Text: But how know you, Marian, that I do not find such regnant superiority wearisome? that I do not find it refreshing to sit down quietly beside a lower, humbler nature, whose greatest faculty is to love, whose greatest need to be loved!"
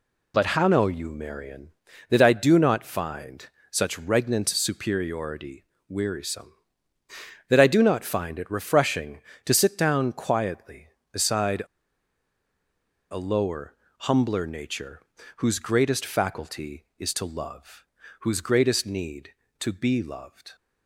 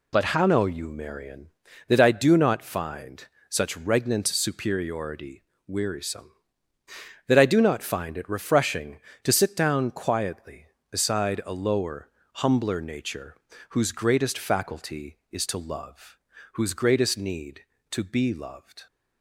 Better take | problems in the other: second | pauses between "find" and "such"; slight; at 3.4 s; 0.24 s long; slight in the second // pauses between "superiority" and "wearisome"; slight; at 5.6 s; 0.24 s long; slight in the second // pauses between "beside" and "a"; strong; at 11.6 s; 1.4 s long

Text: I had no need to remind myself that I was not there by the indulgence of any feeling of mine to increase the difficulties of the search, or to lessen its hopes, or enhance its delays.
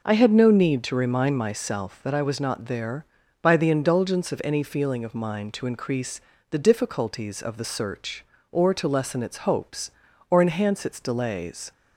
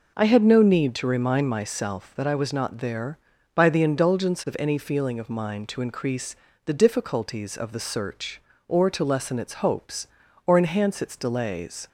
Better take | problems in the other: neither | pauses between "increase" and "the"; slight; the same in both

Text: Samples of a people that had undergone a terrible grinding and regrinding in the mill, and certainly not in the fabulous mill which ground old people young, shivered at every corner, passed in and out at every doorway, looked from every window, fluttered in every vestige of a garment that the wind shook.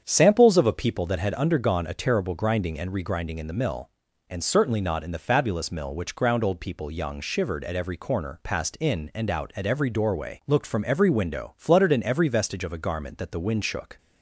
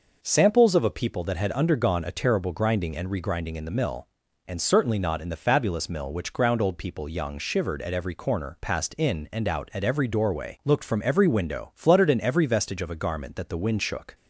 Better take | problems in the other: second | starts louder than the rest; strong; until 1.3 s; 8 dB

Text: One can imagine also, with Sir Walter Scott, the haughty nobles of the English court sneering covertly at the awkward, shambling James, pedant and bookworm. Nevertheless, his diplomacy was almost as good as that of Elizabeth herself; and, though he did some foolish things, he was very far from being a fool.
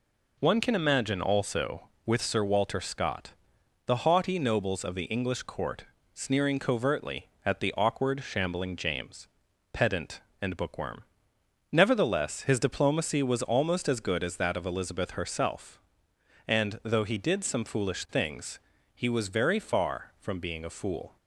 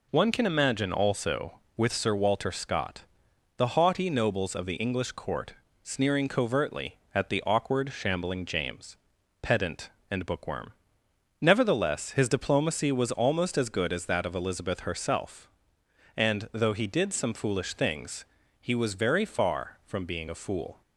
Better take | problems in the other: neither | pauses between "court" and "sneering"; slight; the same in both

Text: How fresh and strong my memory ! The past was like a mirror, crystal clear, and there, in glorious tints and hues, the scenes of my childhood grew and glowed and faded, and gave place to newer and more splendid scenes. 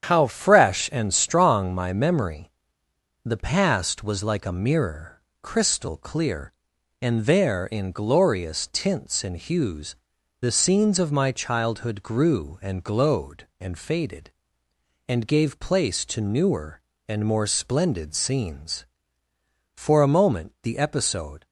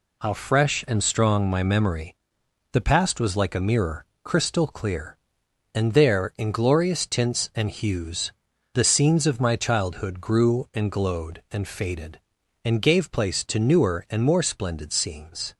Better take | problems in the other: second | starts louder than the rest; strong; until 1.1 s; 8.5 dB // goes on to say "For a moment the episode"; strong; from 19.7 s on; 1.7 s long

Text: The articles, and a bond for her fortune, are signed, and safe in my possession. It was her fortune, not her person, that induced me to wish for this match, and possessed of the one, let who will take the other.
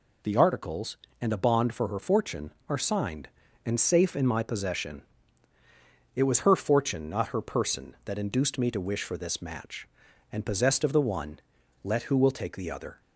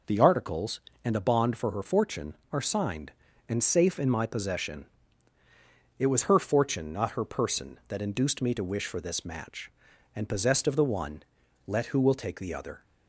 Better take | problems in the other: first | starts louder than the rest; noticeable; until 1.2 s; 5 dB

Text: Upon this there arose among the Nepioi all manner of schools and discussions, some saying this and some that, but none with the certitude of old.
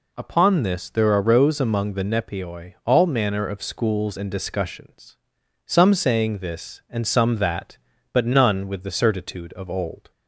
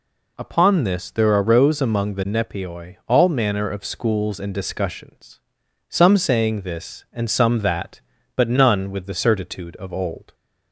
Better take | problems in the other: neither | none

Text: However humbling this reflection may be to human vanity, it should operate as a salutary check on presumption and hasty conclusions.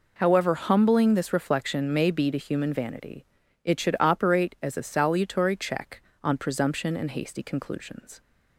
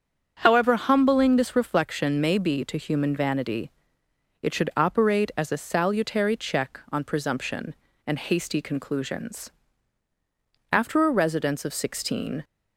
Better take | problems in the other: first | starts louder than the rest; until 1.4 s; 7 dB // goes on to say "After a residence of sixteen"; strong; from 10.7 s on; 1.7 s long

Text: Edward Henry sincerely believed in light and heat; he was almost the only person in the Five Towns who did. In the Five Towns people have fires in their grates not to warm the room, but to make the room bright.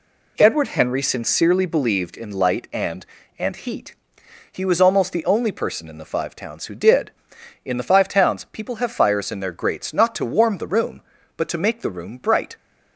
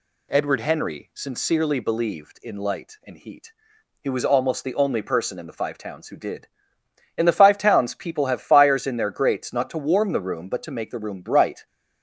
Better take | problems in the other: second | says "and" twice; at 3.3 s

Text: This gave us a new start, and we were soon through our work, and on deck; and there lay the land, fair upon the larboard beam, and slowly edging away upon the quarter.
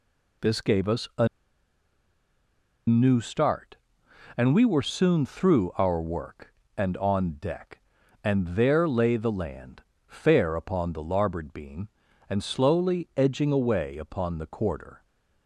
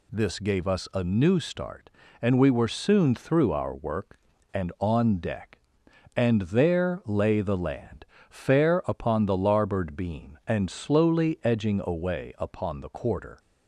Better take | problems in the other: second | pauses between "a" and "new"; strong; at 1.2 s; 1.6 s long

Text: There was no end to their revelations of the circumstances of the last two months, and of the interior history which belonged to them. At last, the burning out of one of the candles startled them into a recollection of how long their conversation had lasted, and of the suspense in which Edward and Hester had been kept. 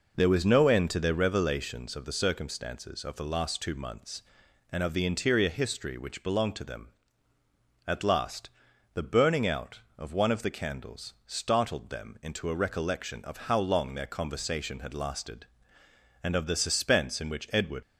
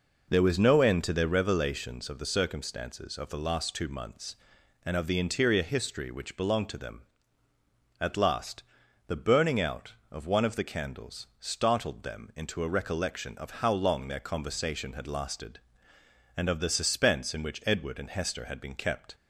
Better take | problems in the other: second | stops before "and Hester had been kept"; at 17.8 s

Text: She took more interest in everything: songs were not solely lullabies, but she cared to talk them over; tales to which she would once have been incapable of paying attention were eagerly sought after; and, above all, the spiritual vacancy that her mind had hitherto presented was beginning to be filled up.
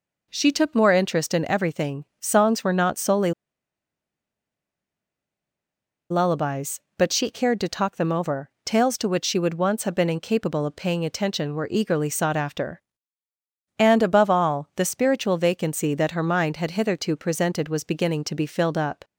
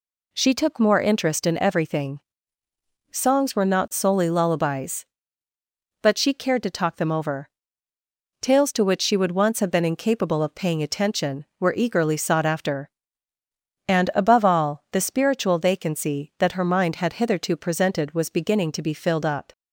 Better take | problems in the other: second | pauses between "solely" and "lullabies"; strong; at 3.3 s; 2.7 s long

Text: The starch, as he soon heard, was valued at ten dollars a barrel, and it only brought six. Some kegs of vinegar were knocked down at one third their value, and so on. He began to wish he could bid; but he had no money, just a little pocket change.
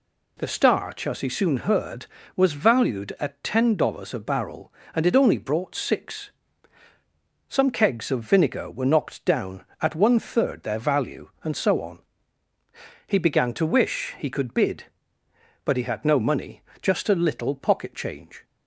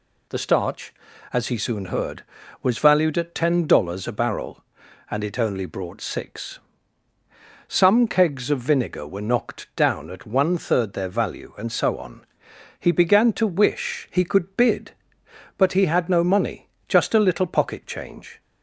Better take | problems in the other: neither | none

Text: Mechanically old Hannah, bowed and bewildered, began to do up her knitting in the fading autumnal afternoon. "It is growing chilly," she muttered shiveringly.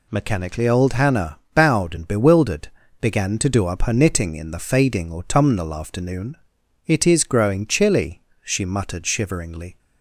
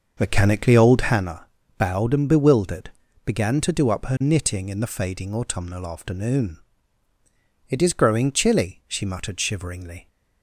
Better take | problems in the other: first | starts louder than the rest; until 1.3 s; 6 dB

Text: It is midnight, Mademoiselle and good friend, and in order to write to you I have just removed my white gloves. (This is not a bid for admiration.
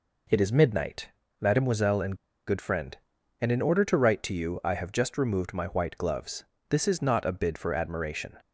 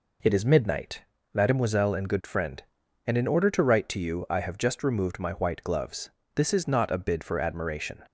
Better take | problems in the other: second | pauses between "and" and "good"; slight; at 2.1 s; 0.33 s long

